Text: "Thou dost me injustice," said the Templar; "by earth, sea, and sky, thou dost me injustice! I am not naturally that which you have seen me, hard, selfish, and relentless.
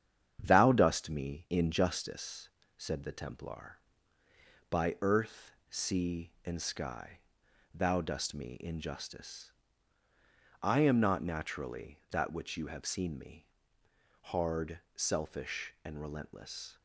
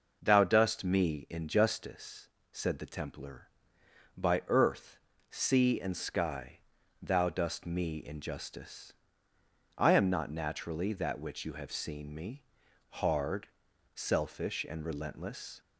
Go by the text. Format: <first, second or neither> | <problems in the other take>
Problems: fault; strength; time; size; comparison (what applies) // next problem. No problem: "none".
second | gets quieter; noticeable; throughout; 5 dB